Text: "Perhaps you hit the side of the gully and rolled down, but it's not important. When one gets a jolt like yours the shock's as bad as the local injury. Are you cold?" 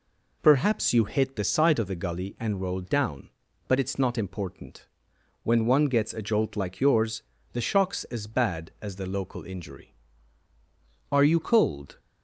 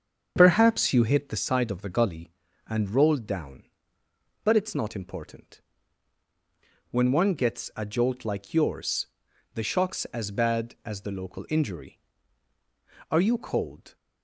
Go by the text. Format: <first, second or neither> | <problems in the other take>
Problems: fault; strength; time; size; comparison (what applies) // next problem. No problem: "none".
first | starts louder than the rest; strong; until 1.7 s; 7 dB // pauses between "yours" and "the"; noticeable; at 9.0 s; 0.48 s long; slight in the first